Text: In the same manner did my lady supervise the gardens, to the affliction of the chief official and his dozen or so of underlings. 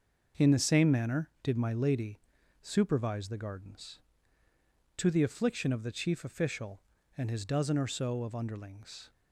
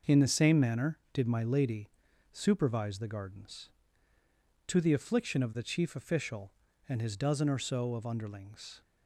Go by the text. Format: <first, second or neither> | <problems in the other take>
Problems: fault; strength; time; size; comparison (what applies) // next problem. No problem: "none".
neither | starts louder than the rest; noticeable; the same in both // pauses between "lady" and "supervise"; the same in both